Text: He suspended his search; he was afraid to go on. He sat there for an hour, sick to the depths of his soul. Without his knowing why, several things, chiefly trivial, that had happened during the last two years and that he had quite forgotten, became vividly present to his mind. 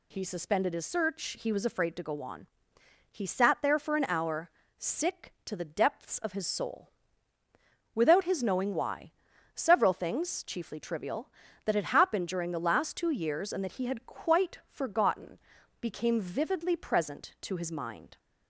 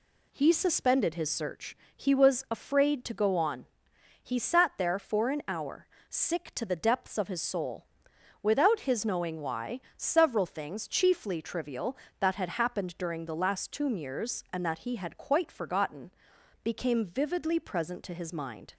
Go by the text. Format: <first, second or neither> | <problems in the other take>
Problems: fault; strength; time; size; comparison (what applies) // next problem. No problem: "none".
first | says "tomb" for "two"; at 13.7 s